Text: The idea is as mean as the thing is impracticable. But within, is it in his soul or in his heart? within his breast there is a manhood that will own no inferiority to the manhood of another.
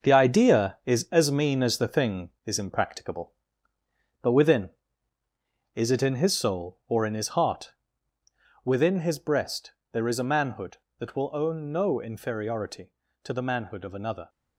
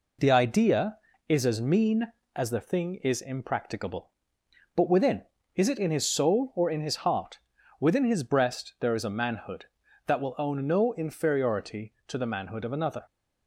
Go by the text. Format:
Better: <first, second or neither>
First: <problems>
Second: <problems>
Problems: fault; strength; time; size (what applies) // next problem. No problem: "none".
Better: second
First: gets quieter; strong; throughout; 8 dB // pauses between "breast" and "there"; slight; at 9.7 s; 0.20 s long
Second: none